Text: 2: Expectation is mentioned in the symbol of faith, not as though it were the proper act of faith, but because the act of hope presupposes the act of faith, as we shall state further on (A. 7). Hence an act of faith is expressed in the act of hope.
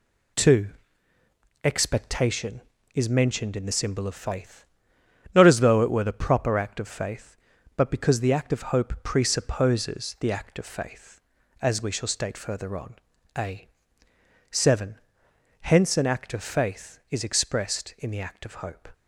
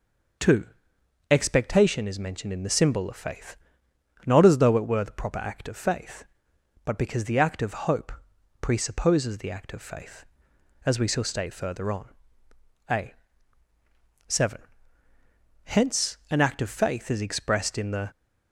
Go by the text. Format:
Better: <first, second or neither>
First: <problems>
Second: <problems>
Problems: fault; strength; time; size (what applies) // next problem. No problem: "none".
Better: first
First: none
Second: pauses between "hope" and "presupposes"; noticeable; at 8.1 s; 0.50 s long // stops before "act of hope"; at 18.1 s